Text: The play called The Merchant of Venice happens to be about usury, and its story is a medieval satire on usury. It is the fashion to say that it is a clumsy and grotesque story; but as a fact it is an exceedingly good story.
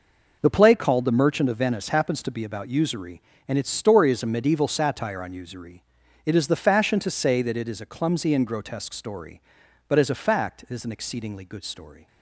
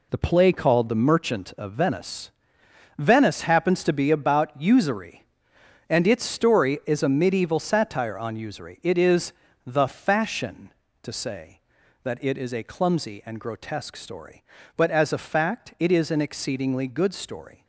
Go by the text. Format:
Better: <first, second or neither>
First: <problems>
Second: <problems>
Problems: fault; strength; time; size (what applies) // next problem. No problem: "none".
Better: first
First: none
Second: says "Venice" twice; at 2.9 s // pauses between "is" and "the"; slight; at 9.3 s; 0.32 s long